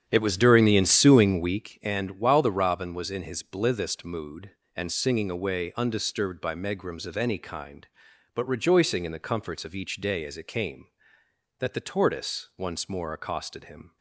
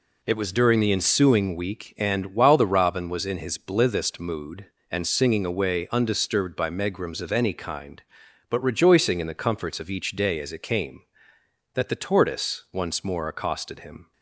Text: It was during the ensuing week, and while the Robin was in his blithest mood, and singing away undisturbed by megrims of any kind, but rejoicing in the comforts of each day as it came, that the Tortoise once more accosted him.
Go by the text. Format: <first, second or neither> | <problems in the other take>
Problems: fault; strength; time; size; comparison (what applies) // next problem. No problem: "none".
second | starts louder than the rest; strong; until 1.7 s; 9 dB